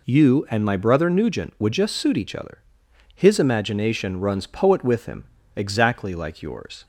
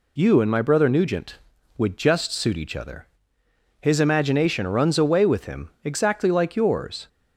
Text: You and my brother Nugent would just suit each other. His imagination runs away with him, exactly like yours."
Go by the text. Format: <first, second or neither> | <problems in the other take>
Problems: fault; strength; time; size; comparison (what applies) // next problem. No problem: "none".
second | says "poet" for "away"; at 4.4 s